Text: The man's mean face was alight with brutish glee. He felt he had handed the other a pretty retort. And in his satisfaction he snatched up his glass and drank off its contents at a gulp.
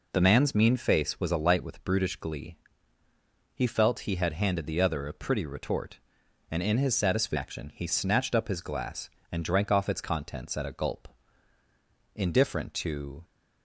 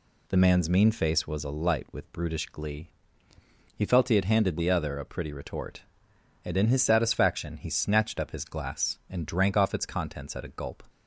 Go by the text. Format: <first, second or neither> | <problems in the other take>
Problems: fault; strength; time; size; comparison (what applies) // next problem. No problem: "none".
second | goes on to say "Indifferent to"; noticeable; from 12.1 s on; 1.1 s long